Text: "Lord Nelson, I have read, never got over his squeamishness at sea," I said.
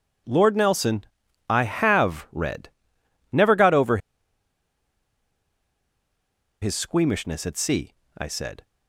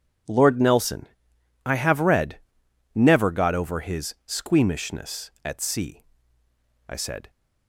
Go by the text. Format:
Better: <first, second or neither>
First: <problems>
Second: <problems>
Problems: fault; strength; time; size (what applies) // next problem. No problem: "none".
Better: second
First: pauses between "over" and "his"; strong; at 3.9 s; 2.6 s long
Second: none